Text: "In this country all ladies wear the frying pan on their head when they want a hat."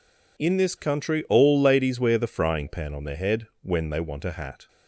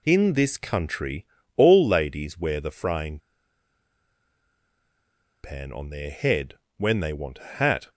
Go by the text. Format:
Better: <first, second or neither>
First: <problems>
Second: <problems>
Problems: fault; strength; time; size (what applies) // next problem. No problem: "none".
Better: first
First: none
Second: pauses between "country" and "all"; slight; at 1.2 s; 0.30 s long // pauses between "frying" and "pan"; strong; at 3.1 s; 2.2 s long // pauses between "head" and "when"; slight; at 6.5 s; 0.22 s long